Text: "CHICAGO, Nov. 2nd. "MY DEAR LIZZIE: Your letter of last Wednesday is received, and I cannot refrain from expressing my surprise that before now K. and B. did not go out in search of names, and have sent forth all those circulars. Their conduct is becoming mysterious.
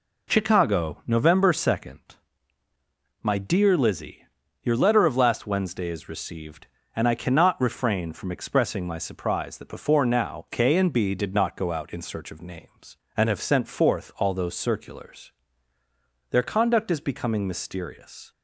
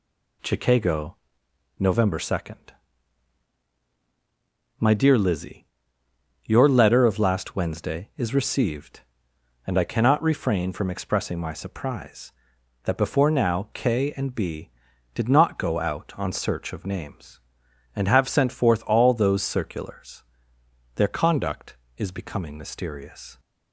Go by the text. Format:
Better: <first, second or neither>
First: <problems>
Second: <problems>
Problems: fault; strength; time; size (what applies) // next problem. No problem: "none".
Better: first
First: none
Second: says "on" for "in"; at 16.1 s